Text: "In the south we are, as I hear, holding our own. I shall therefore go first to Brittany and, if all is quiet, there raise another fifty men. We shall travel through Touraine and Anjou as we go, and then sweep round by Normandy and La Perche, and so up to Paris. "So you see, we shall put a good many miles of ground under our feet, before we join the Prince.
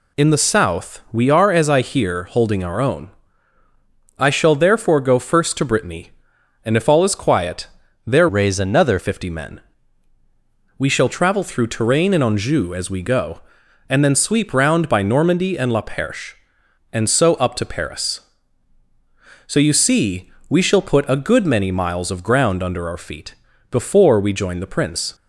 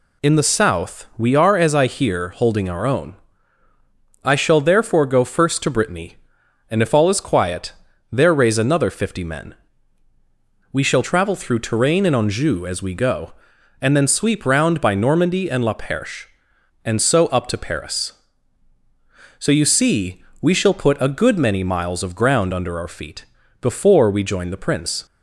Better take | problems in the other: second | changes voice from "raise" to "another"; from 8.2 to 8.9 s; 0.7 s long

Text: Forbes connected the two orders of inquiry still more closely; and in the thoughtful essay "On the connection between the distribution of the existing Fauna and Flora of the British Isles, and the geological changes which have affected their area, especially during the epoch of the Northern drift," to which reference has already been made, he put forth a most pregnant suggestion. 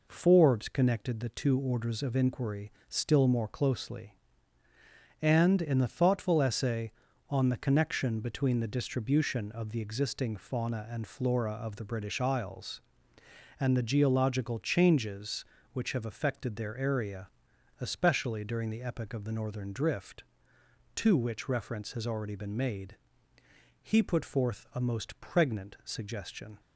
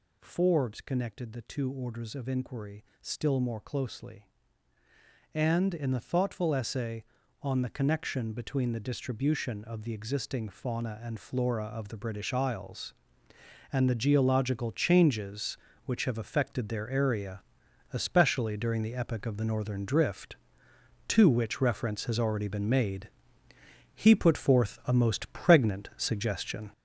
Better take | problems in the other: first | gets louder; throughout; 6.5 dB // pauses between "inquiry" and "still"; slight; at 2.8 s; 0.16 s long; slight in the first

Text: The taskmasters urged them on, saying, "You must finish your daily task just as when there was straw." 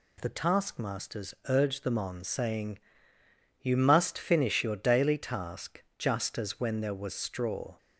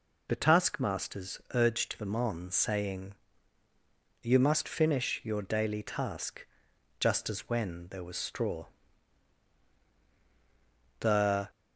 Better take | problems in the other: first | pauses between "task" and "just"; noticeable; at 6.4 s; 0.52 s long; slight in the first // goes on to say "The"; from 10.9 s on; 0.50 s long

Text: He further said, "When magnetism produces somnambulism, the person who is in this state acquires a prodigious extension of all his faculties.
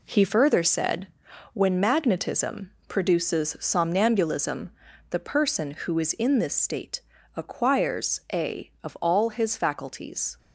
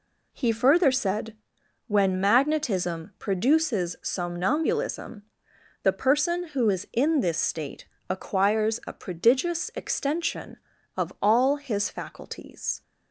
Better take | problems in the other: second | pauses between "magnetism" and "produces"; slight; at 2.7 s; 0.16 s long // pauses between "state" and "acquires"; slight; at 6.9 s; 0.36 s long; slight in the second // skips "prodigious extension"; at 8.7 s

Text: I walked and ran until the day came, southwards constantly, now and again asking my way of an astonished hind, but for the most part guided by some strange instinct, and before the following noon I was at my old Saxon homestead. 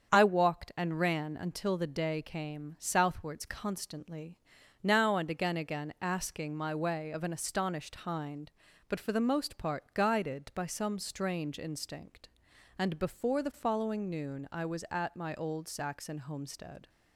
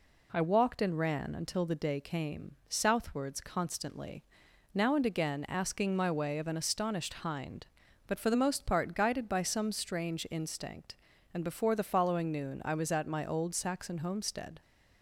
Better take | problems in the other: second | starts louder than the rest; strong; until 1.1 s; 7.5 dB // says "again" twice; at 5.5 s

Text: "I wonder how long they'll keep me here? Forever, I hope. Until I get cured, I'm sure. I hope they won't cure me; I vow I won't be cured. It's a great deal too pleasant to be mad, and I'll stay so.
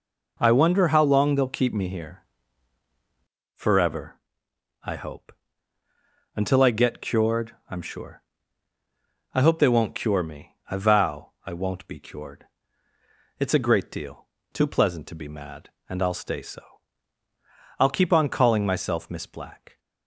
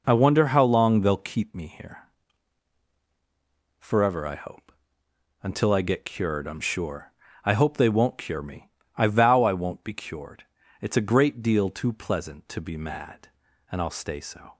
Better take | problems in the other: second | pauses between "vow" and "I"; slight; at 11.3 s; 0.16 s long // pauses between "deal" and "too"; slight; at 14.2 s; 0.26 s long // goes on to say "I'll keep on calling myself Miss Black"; strong; from 17.7 s on; 2.0 s long

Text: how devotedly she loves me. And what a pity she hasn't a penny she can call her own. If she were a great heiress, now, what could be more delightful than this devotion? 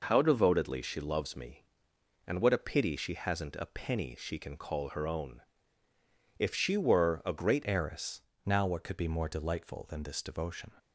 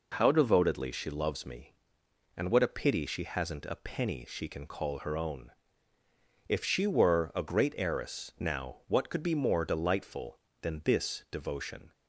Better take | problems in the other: second | changes voice at "heiress"; from 7.6 s on; 3.1 s long

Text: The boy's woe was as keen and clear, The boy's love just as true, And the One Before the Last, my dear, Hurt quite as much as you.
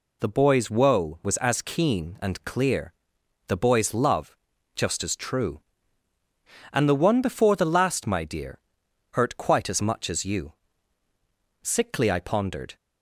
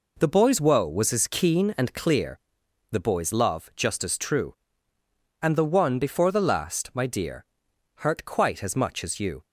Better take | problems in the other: second | pauses between "love" and "just"; at 4.3 s; 0.40 s long // goes on to say "Sickly I pondered"; noticeable; from 11.6 s on; 1.1 s long

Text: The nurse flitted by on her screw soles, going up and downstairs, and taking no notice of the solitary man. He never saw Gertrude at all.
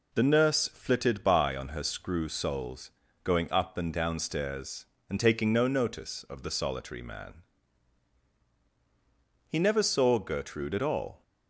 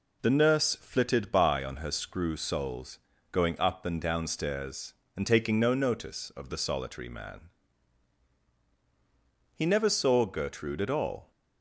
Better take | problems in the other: neither | none

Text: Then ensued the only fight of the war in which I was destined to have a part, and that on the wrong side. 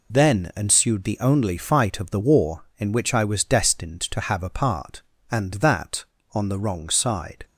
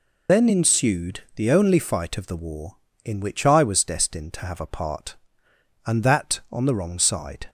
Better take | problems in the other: first | loses the start of "Then"; at 0.2 s; 150 ms

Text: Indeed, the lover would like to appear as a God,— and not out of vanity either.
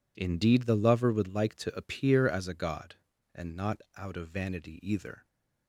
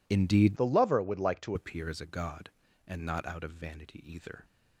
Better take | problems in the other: first | changes voice from "the" to "to"; from 0.5 to 1.5 s; 1.0 s long

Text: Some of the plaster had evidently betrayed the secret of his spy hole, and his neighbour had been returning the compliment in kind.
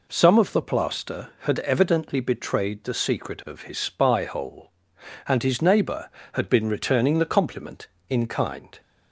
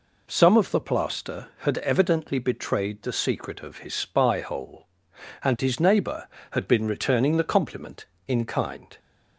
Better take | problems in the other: neither | none

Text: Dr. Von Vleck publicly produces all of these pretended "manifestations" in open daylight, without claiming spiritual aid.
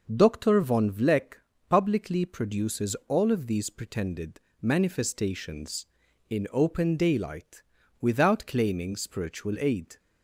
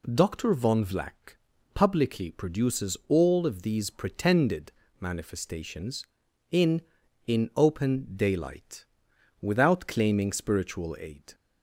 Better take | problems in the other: first | pauses between "Vleck" and "publicly"; slight; at 1.3 s; 0.34 s long; slight in the first // pauses between "pretended" and "manifestations"; slight; at 4.7 s; 0.26 s long; slight in the first // says "in" twice; at 7.2 s

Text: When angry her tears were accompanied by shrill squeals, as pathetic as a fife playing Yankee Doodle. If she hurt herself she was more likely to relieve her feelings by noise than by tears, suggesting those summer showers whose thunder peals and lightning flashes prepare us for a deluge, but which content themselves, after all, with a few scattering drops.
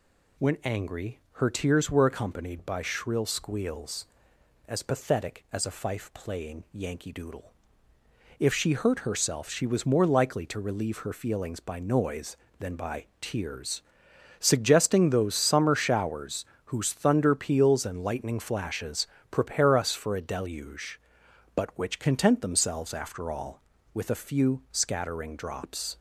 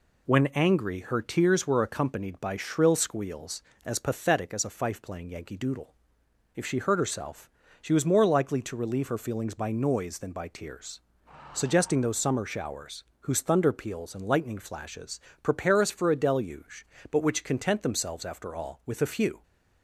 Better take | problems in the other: first | pauses between "herself" and "she"; slight; at 7.4 s; 0.32 s long // pauses between "showers" and "whose"; slight; at 13.0 s; 0.16 s long; slight in the first // pauses between "flashes" and "prepare"; slight; at 15.2 s; 0.24 s long; slight in the first // stops before "scattering drops"; at 19.4 s

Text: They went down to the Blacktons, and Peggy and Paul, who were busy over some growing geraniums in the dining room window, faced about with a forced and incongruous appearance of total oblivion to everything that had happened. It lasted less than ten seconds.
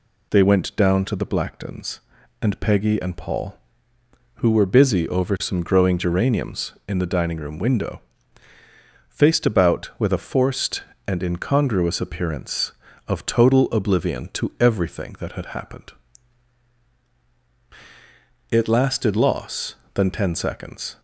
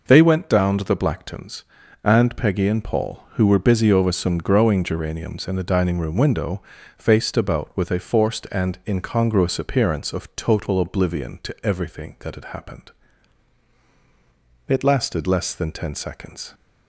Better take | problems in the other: second | says "loss" for "less"; at 19.1 s

